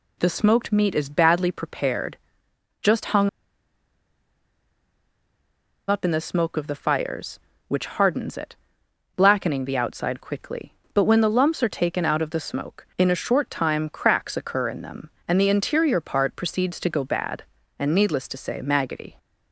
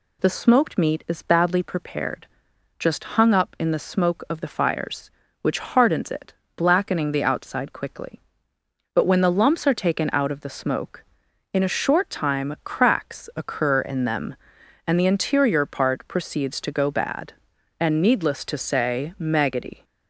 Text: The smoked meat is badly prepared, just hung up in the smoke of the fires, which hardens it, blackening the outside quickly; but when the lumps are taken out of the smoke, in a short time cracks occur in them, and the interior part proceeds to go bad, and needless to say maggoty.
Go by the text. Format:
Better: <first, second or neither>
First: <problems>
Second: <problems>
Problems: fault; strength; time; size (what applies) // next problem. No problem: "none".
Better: second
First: pauses between "hung" and "up"; strong; at 3.2 s; 2.6 s long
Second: none